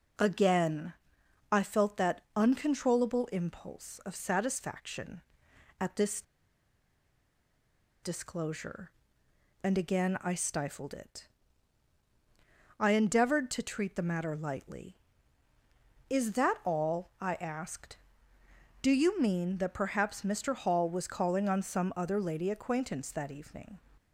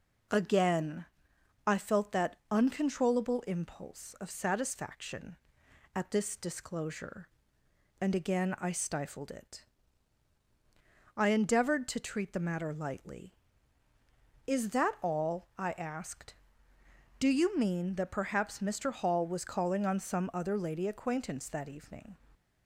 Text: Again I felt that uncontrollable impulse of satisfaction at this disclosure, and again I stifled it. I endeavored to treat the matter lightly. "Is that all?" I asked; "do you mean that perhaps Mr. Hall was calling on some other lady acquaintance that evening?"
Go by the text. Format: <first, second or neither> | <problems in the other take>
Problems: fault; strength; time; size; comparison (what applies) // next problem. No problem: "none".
second | pauses between "Again" and "I"; noticeable; at 0.9 s; 0.58 s long; noticeable in the second // pauses between "this" and "disclosure"; strong; at 6.2 s; 1.8 s long